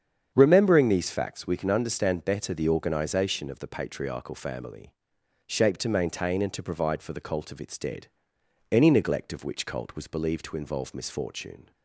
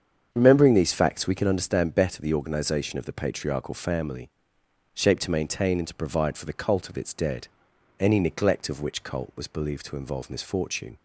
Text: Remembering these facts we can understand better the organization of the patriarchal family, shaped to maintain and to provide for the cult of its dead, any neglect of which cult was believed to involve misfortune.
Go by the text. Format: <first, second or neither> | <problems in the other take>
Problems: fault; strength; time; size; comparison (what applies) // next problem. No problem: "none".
neither | starts louder than the rest; strong; the same in both